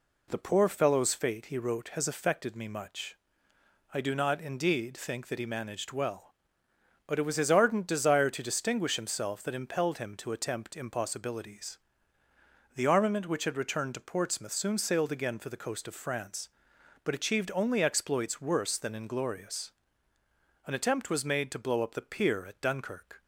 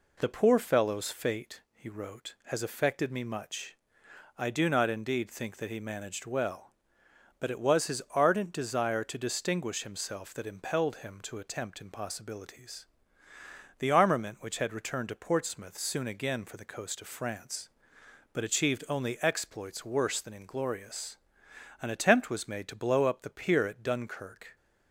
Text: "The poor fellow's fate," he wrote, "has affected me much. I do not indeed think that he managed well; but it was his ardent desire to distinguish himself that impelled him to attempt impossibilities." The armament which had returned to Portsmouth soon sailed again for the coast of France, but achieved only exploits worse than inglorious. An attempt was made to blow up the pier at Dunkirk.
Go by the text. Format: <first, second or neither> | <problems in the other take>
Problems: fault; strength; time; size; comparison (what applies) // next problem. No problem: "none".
first | skips "sailed"; at 16.0 s